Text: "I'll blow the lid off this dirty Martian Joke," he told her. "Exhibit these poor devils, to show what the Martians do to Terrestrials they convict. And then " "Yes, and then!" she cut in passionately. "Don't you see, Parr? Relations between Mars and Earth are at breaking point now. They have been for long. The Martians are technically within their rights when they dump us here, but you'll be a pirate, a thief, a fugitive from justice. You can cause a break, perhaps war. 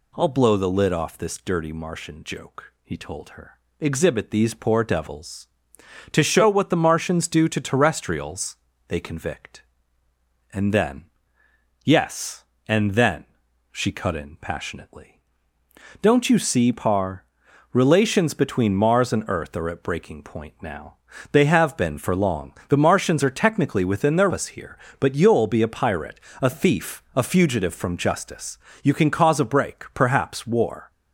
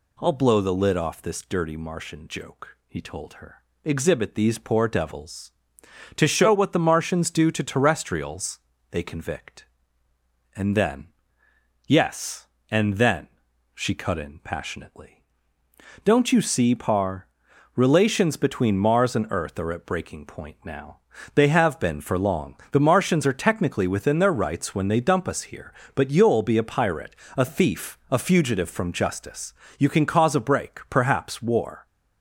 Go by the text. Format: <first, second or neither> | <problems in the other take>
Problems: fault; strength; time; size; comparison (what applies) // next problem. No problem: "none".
second | pauses between "Terrestrials" and "they"; slight; at 8.5 s; 0.32 s long; slight in the second // skips "rights when they dump"; at 24.3 s